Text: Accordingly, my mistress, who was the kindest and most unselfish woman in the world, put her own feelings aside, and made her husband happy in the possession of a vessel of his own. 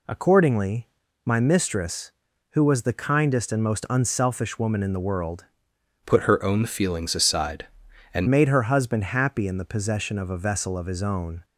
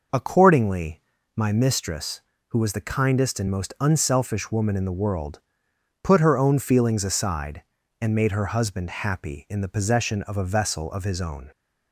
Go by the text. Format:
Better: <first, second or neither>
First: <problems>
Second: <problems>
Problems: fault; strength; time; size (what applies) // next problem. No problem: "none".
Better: second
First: changes voice from "put" to "and"; from 6.0 to 8.2 s; 2.2 s long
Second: none